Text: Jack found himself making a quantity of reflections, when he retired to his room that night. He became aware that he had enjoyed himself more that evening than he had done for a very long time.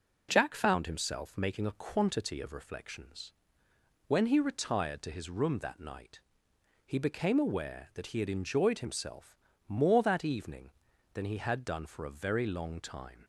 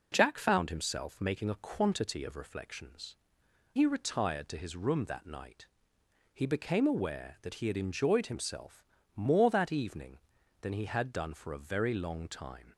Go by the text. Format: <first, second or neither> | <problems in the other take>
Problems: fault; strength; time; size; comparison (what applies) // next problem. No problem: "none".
first | skips "when"; at 3.4 s // pauses between "himself" and "more"; slight; at 8.8 s; 0.32 s long; slight in the first